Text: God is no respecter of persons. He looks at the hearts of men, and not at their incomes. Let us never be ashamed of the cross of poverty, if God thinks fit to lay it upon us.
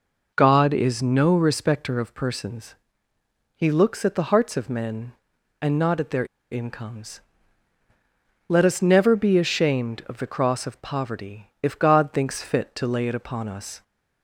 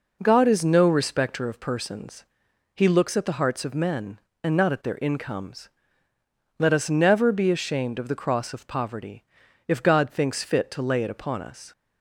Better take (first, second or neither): second